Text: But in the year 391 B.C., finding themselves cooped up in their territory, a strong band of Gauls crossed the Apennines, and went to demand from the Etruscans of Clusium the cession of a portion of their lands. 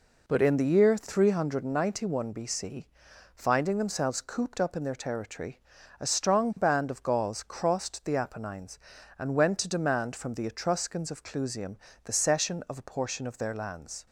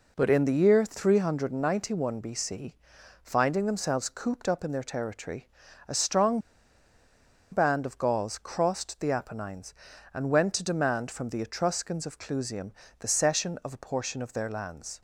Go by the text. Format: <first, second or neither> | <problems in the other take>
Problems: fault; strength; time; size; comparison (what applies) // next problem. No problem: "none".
first | pauses between "strong" and "band"; at 6.3 s; 1.1 s long // pauses between "Clusium" and "the"; slight; at 12.7 s; 0.26 s long; slight in the first